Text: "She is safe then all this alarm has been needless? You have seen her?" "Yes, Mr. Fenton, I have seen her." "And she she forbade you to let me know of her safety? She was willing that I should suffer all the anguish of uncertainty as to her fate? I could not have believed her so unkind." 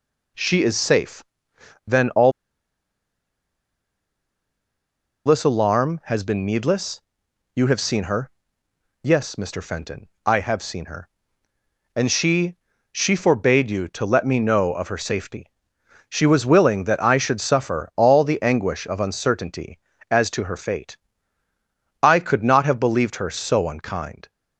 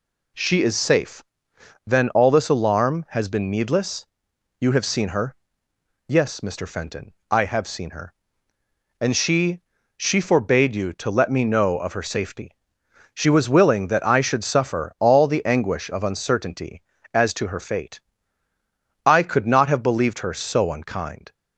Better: second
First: pauses between "safe" and "then"; noticeable; at 1.2 s; 0.64 s long // pauses between "all" and "this"; strong; at 2.3 s; 2.9 s long // pauses between "she" and "she"; slight; at 12.5 s; 0.34 s long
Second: pauses between "safe" and "then"; noticeable; at 1.2 s; 0.64 s long // pauses between "she" and "she"; slight; at 9.6 s; 0.34 s long

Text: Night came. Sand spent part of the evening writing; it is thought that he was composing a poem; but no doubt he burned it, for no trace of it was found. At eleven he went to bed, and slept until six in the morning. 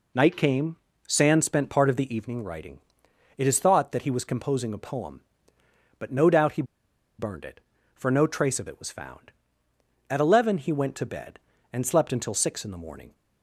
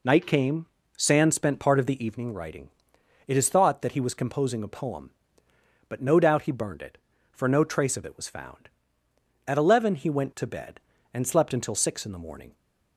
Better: second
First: pauses between "he" and "burned"; noticeable; at 6.6 s; 0.55 s long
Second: none

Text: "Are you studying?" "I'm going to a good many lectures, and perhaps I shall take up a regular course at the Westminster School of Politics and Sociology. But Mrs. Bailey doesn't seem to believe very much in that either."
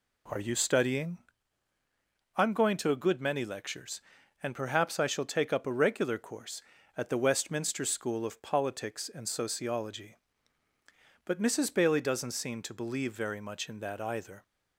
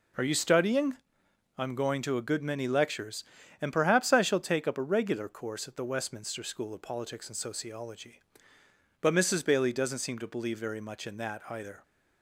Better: neither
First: none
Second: none

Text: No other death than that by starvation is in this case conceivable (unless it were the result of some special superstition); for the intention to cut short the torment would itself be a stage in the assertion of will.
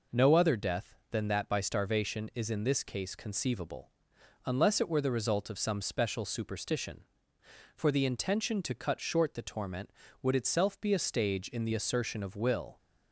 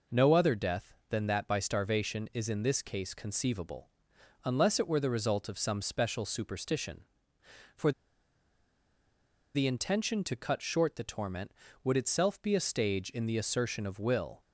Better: first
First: none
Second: pauses between "for" and "the"; strong; at 7.9 s; 1.6 s long

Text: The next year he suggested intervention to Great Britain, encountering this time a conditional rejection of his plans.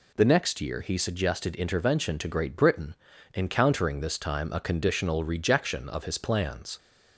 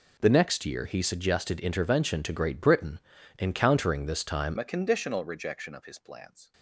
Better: first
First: none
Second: changes voice at "a"; from 4.5 s on; 2.0 s long

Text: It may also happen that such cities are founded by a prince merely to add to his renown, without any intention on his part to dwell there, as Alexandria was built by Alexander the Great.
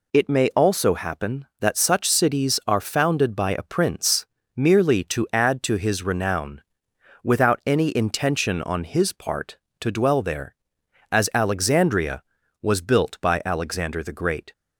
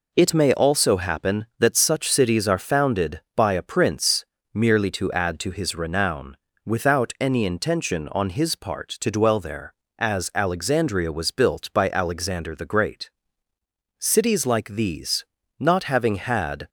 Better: first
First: pauses between "prince" and "merely"; slight; at 4.2 s; 0.32 s long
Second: pauses between "prince" and "merely"; slight; at 4.2 s; 0.30 s long // goes on to say "Cities like these not having had"; strong; from 13.9 s on; 2.7 s long

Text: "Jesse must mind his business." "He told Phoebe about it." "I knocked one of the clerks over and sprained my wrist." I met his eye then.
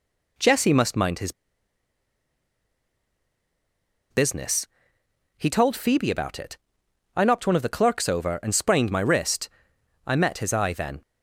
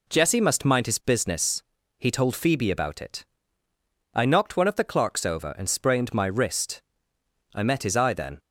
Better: second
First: pauses between "his" and "business"; strong; at 1.3 s; 2.7 s long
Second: none

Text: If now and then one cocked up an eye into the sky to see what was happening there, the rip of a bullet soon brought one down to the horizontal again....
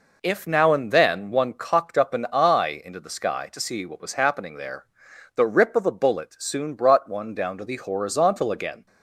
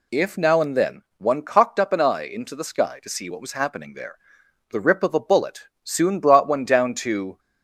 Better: first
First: none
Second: pauses between "then" and "one"; slight; at 1.0 s; 0.16 s long // pauses between "bullet" and "soon"; slight; at 5.6 s; 0.20 s long // stops before "the horizontal again"; at 7.3 s

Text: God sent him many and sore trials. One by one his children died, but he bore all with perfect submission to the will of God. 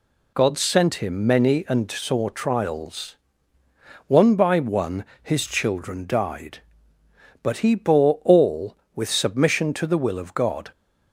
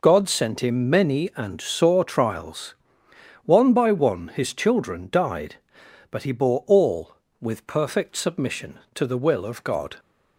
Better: second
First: pauses between "one" and "his"; slight; at 5.0 s; 0.18 s long // skips "perfect"; at 9.0 s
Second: none

